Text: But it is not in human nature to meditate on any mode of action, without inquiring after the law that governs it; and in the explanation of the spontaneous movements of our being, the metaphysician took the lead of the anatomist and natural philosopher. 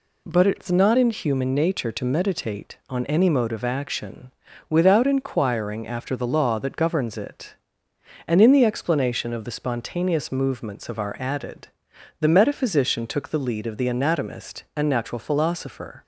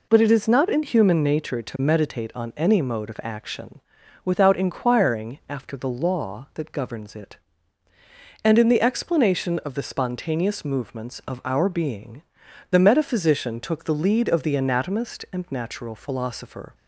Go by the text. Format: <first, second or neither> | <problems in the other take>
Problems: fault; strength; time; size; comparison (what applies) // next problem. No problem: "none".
second | says "added" for "being"; at 11.2 s